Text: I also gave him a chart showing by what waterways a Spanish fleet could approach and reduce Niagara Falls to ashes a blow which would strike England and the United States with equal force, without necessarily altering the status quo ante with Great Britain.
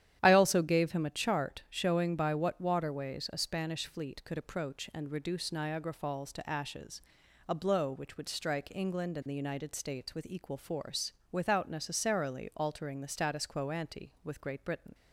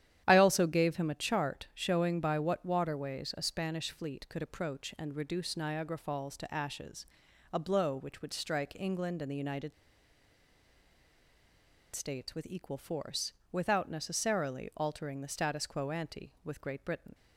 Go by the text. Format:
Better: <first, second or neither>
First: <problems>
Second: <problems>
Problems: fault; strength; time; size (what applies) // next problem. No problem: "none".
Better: first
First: starts louder than the rest; strong; until 1.2 s; 10.5 dB // pauses between "ashes" and "a"; noticeable; at 7.0 s; 0.46 s long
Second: starts louder than the rest; strong; until 1.2 s; 10.5 dB // pauses between "ashes" and "a"; noticeable; at 7.0 s; 0.46 s long // pauses between "United" and "States"; strong; at 9.7 s; 2.2 s long